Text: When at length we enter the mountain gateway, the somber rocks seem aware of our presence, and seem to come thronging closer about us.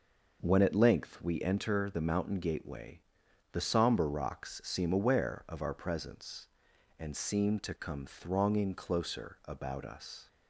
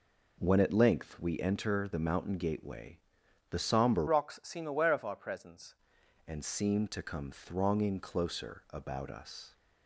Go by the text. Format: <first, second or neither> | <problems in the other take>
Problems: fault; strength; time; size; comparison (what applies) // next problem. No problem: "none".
first | changes voice from "rocks" to "presence"; from 4.0 to 5.7 s; 1.7 s long